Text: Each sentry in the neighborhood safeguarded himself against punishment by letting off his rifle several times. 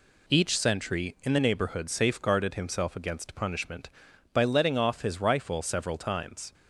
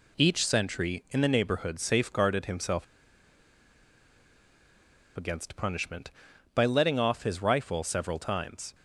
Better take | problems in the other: first | pauses between "himself" and "against"; strong; at 2.8 s; 2.3 s long

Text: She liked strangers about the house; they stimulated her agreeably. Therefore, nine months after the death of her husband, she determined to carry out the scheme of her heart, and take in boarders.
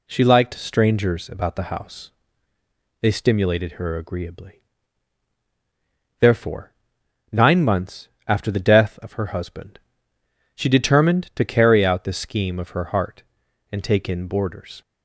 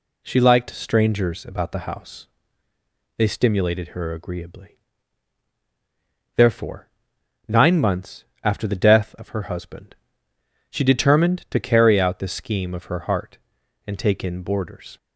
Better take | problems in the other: neither | pauses between "months" and "after"; slight; the same in both

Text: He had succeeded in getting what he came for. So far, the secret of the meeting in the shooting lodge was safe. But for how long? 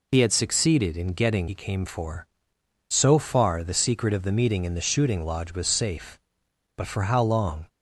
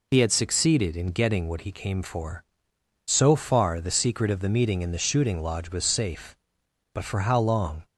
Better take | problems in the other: second | skips "what"; at 1.4 s

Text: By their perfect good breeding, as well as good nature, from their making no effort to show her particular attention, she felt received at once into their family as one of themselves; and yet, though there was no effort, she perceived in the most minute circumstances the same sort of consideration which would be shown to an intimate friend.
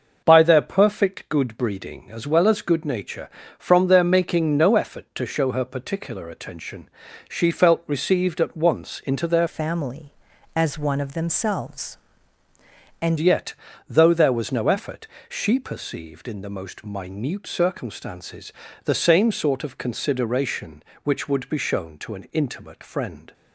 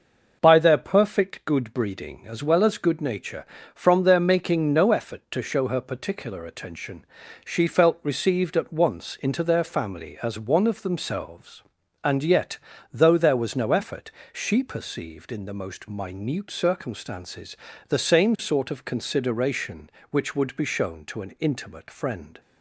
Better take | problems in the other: second | starts louder than the rest; noticeable; until 1.2 s; 6 dB; noticeable in the second // changes voice from "family" to "and"; from 9.4 to 13.1 s; 3.7 s long // pauses between "circumstances" and "the"; slight; at 18.5 s; 0.32 s long; slight in the second

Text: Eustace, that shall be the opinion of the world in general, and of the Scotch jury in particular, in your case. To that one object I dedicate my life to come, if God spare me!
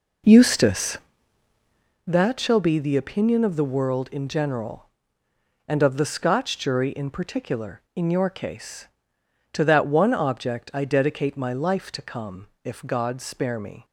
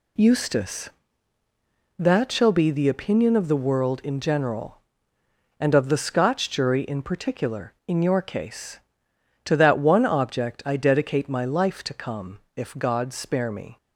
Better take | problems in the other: second | starts louder than the rest; noticeable; until 2.1 s; 4.5 dB

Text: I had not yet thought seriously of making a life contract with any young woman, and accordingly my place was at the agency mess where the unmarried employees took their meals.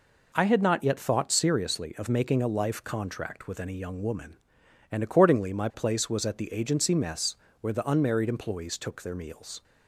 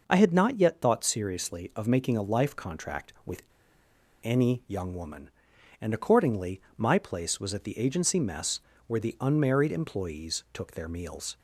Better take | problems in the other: first | pauses between "with" and "any"; noticeable; at 3.4 s; 0.81 s long // pauses between "accordingly" and "my"; slight; at 6.5 s; 0.16 s long // pauses between "mess" and "where"; slight; at 8.5 s; 0.26 s long; slight in the first

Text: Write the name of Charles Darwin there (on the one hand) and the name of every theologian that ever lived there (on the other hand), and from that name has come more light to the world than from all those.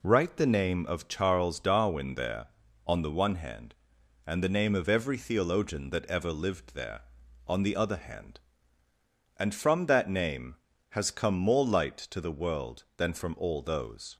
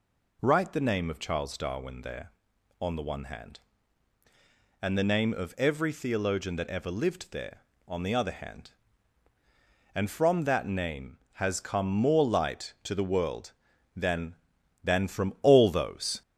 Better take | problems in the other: first | says "than" twice; at 14.8 s

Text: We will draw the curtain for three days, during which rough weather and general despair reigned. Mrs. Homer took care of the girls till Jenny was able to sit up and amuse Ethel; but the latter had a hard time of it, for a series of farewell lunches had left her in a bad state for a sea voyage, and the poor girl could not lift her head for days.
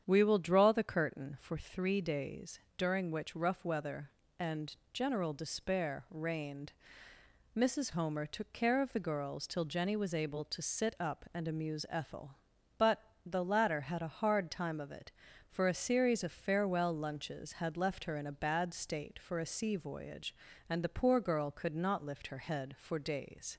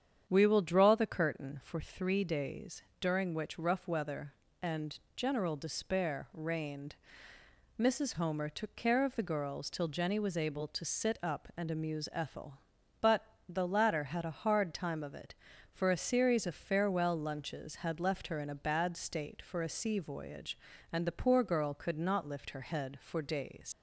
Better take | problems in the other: first | starts louder than the rest; strong; until 1.2 s; 8.5 dB; strong in the first // pauses between "and" and "general"; slight; at 4.9 s; 0.16 s long; slight in the first // pauses between "but" and "the"; slight; at 13.2 s; 0.24 s long; slight in the first // leaves "days" unfinished; at 23.7 s; 70 ms

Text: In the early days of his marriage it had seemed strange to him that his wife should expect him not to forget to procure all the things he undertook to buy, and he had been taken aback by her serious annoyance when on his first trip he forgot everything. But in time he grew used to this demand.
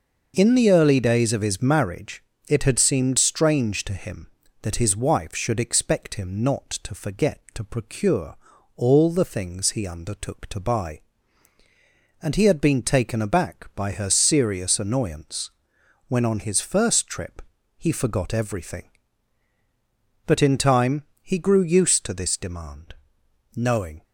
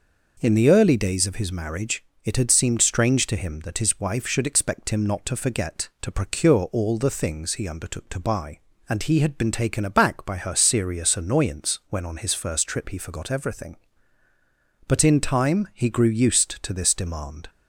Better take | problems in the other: second | pauses between "marriage" and "it"; slight; at 2.2 s; 0.28 s long; slight in the second // pauses between "procure" and "all"; at 8.3 s; 0.40 s long // pauses between "annoyance" and "when"; noticeable; at 15.5 s; 0.56 s long // pauses between "trip" and "he"; slight; at 17.4 s; 0.34 s long // pauses between "time" and "he"; slight; at 21.0 s; 0.18 s long // goes on to say "Knowing"; slight; from 23.5 s on; 0.48 s long

